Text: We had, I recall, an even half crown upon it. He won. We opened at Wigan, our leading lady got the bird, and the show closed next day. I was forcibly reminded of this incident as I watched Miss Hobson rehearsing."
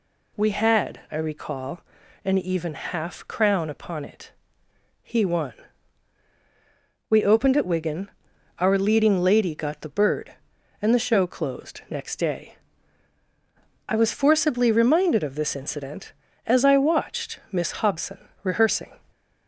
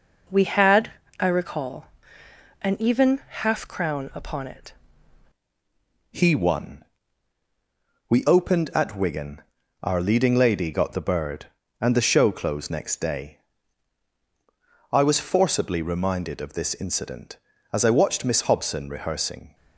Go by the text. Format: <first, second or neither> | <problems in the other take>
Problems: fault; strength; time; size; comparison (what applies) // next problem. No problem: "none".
first | changes voice at "He"; from 6.1 s on; 13.4 s long